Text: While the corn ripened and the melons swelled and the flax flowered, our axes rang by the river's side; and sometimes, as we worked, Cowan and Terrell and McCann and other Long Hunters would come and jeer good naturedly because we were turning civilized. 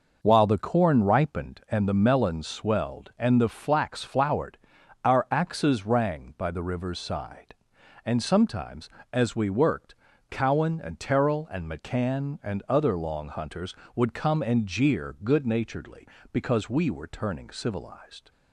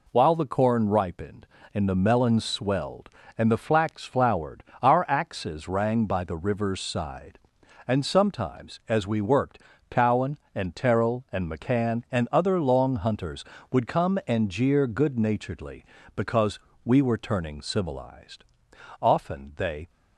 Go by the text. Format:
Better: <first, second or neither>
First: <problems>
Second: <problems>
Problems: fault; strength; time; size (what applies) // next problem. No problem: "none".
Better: first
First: none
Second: pauses between "because" and "we"; slight; at 16.5 s; 0.26 s long // goes on to say "Often they"; noticeable; from 19.0 s on; 0.88 s long